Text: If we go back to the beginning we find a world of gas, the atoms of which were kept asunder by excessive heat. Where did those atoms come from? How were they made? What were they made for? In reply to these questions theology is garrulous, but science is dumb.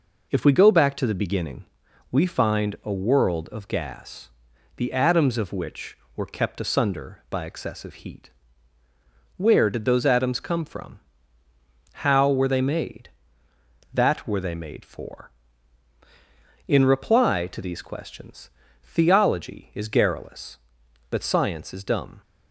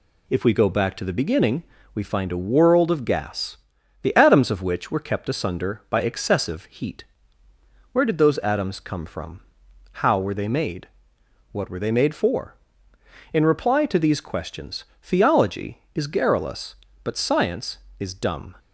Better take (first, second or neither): second